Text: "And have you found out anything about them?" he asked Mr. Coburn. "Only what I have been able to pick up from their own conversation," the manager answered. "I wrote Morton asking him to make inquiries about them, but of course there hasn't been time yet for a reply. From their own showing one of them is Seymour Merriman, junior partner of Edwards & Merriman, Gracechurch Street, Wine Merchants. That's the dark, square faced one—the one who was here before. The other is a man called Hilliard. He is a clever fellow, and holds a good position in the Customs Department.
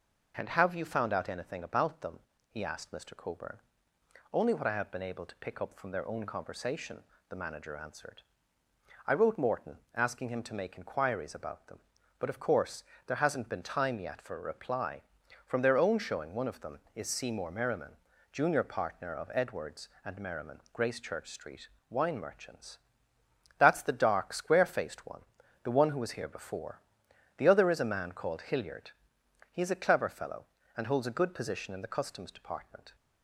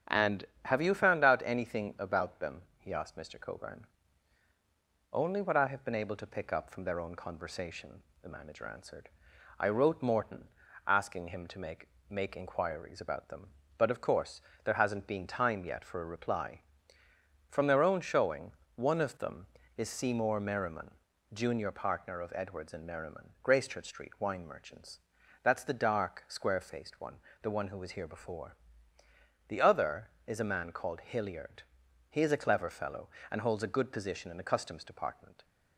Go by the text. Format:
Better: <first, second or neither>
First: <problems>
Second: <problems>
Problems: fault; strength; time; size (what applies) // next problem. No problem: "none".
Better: first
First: pauses between "course" and "there"; slight; at 12.8 s; 0.24 s long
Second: starts louder than the rest; strong; until 1.2 s; 9 dB // pauses between "Morton" and "asking"; at 10.4 s; 0.38 s long // says "make" twice; at 12.0 s // pauses between "course" and "there"; slight; at 14.4 s; 0.22 s long // pauses between "showing" and "one"; slight; at 18.5 s; 0.22 s long